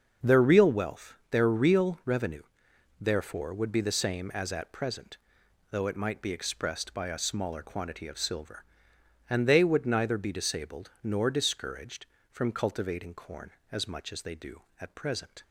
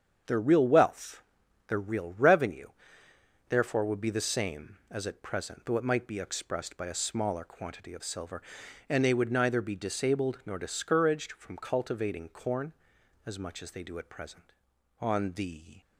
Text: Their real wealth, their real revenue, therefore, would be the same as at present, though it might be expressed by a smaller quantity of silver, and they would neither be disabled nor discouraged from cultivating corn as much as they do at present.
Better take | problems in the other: first | starts louder than the rest; strong; until 1.7 s; 7.5 dB; also in the first // goes on to say "On the"; noticeable; from 15.0 s on; 0.80 s long

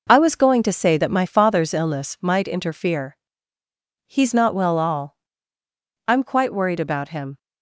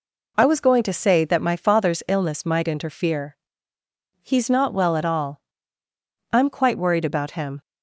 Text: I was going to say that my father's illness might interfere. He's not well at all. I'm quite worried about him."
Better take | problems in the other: second | skips "at"; at 4.7 s

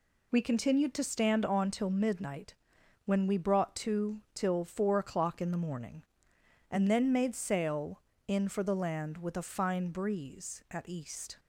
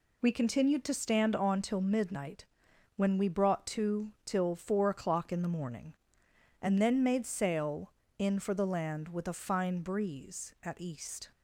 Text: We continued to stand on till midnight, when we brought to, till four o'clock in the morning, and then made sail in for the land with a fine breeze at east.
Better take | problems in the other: neither | none

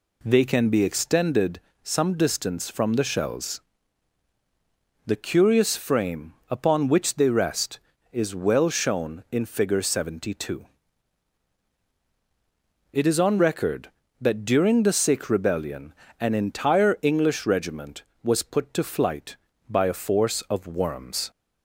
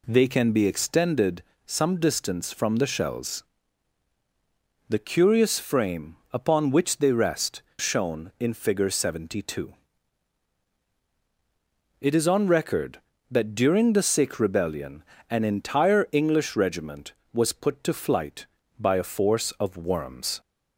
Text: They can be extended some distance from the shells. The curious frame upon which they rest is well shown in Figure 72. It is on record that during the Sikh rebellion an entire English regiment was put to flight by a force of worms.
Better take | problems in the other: first | pauses between "extended" and "some"; slight; at 1.4 s; 0.22 s long; slight in the first // skips "is well"; at 7.7 s // pauses between "rebellion" and "an"; slight; at 15.0 s; 0.26 s long; slight in the first

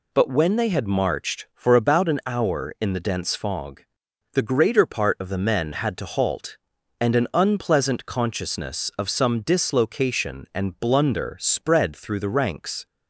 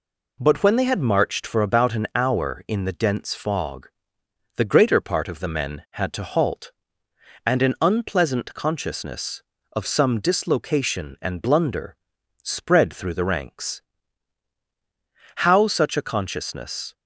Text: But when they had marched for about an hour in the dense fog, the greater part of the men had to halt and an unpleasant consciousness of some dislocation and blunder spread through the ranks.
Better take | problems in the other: first | pauses between "blunder" and "spread"; noticeable; at 11.9 s; 0.48 s long // goes on to say "How such a consciousness"; from 15.3 s on; 1.5 s long

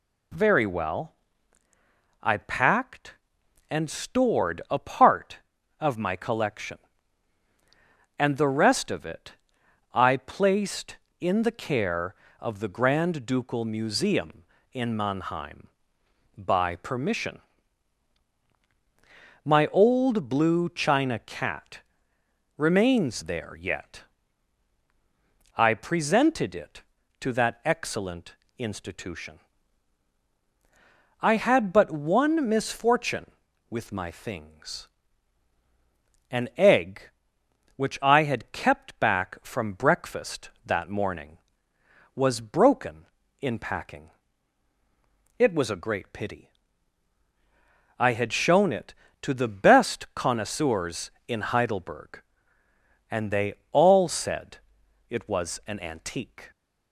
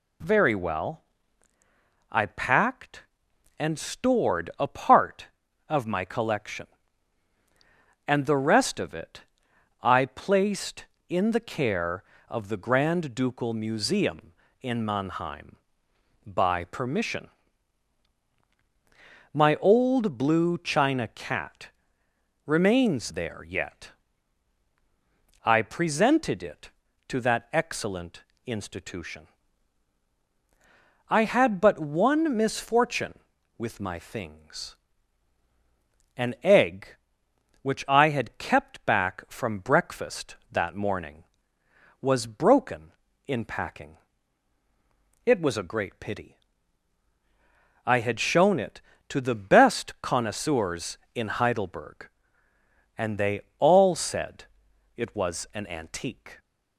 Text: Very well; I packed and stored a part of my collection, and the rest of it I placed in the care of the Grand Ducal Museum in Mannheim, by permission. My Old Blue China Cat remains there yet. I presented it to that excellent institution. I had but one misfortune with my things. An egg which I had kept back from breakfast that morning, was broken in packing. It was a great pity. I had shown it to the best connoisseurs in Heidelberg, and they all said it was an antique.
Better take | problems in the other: neither | pauses between "it" and "I"; noticeable; the same in both // pauses between "Cat" and "remains"; noticeable; the same in both // pauses between "excellent" and "institution"; slight; the same in both // pauses between "they" and "all"; slight; the same in both // pauses between "said" and "it"; noticeable; the same in both

